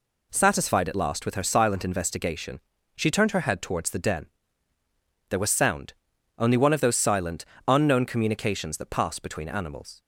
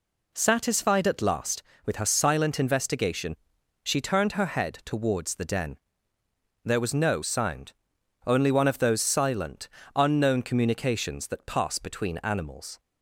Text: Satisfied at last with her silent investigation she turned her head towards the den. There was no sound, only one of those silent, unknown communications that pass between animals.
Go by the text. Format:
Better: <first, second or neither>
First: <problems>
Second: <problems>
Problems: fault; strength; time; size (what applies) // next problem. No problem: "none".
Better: second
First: pauses between "investigation" and "she"; slight; at 2.5 s; 0.36 s long // skips "no"; at 5.5 s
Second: pauses between "investigation" and "she"; noticeable; at 3.3 s; 0.46 s long